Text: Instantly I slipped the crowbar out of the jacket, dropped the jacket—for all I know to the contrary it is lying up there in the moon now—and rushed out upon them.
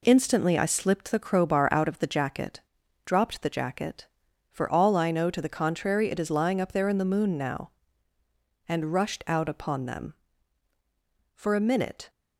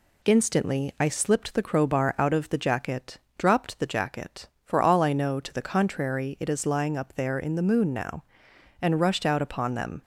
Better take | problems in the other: second | goes on to say "For a minute"; noticeable; from 11.3 s on; 0.76 s long

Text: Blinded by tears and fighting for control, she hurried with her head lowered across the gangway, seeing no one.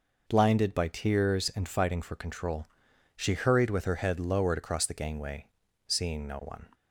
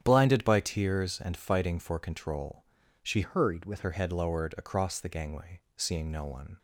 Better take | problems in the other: first | starts louder than the rest; strong; until 1.0 s; 10 dB // changes voice from "hurried" to "with"; from 3.2 to 3.8 s; 0.6 s long

